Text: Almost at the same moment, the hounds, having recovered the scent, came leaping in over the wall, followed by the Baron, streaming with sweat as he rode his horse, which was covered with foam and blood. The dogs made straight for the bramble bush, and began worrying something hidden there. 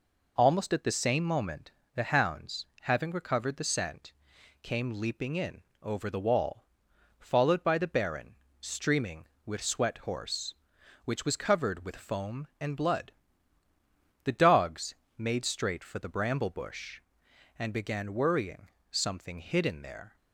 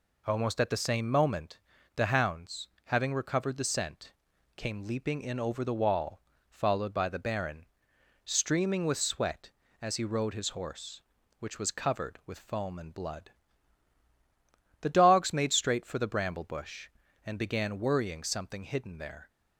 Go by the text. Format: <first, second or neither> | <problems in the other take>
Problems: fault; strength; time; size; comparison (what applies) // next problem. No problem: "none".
second | pauses between "in" and "over"; slight; at 5.6 s; 0.20 s long // skips "as he rode his"; at 9.9 s // pauses between "dogs" and "made"; slight; at 14.9 s; 0.22 s long // pauses between "worrying" and "something"; slight; at 18.6 s; 0.22 s long